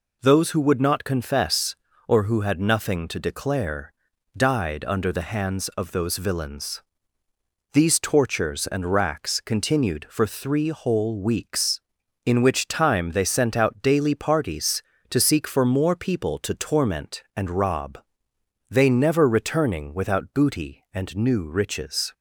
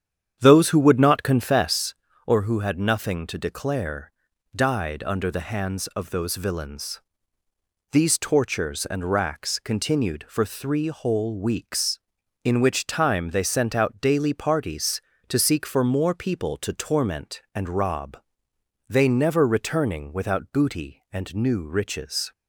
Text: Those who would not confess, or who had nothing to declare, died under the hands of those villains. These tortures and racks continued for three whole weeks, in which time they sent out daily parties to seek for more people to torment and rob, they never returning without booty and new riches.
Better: first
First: none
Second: starts louder than the rest; strong; until 1.7 s; 9 dB

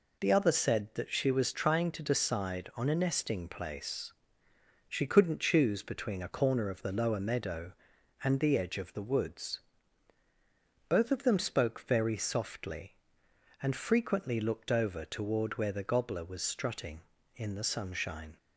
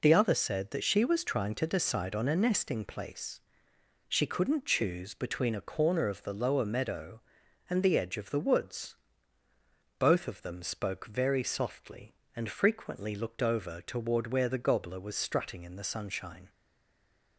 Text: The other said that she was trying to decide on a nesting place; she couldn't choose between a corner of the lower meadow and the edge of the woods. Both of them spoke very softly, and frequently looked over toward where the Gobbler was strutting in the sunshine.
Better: first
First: none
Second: stays silent after the last word; slight; from 16.4 s on; 0.9 s long

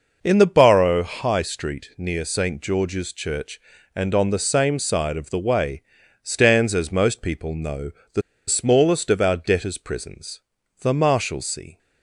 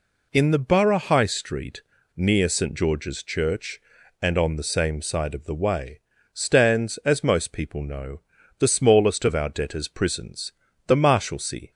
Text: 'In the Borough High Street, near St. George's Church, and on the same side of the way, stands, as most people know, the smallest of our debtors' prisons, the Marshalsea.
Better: second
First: pauses between "the" and "smallest"; slight; at 8.2 s; 0.26 s long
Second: none

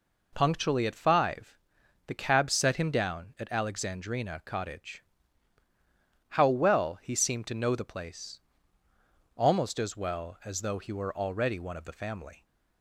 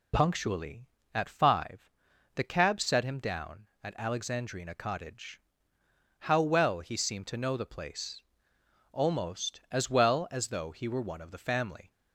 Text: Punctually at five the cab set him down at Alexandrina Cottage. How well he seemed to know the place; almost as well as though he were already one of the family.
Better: first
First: pauses between "five" and "the"; noticeable; at 1.5 s; 0.52 s long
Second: pauses between "five" and "the"; noticeable; at 1.9 s; 0.46 s long // skips "already"; at 11.0 s

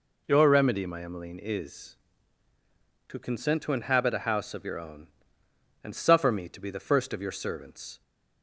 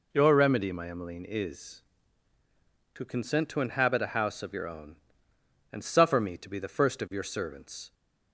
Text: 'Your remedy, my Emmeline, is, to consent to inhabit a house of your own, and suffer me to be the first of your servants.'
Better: neither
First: none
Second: none

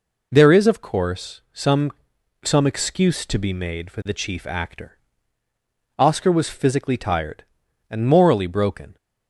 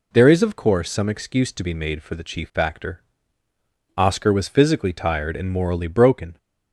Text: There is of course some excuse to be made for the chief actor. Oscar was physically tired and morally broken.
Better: second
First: says "some" twice; at 2.4 s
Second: none

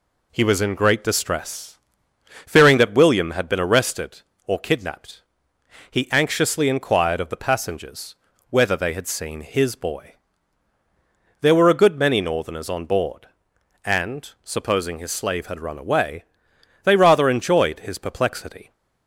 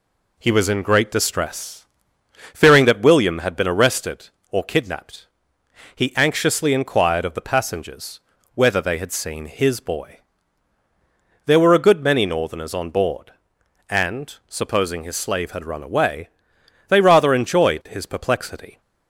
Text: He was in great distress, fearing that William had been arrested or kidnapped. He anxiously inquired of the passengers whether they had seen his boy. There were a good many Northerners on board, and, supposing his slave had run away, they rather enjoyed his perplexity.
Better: neither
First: pauses between "passengers" and "whether"; slight; at 8.1 s; 0.36 s long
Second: pauses between "passengers" and "whether"; slight; at 8.1 s; 0.36 s long

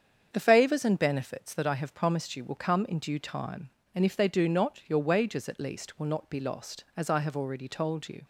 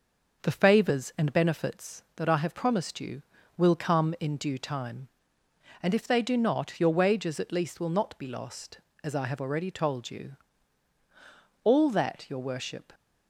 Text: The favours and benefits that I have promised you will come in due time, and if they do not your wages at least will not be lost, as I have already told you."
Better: first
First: starts louder than the rest; strong; until 1.3 s; 7.5 dB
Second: starts louder than the rest; noticeable; until 1.4 s; 6 dB // goes on to say "All that your worship"; from 11.6 s on; 1.3 s long

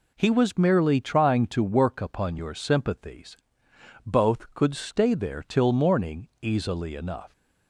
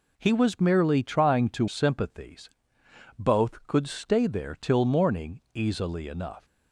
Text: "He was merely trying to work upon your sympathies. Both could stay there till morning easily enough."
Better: first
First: none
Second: skips "work upon your"; at 1.6 s

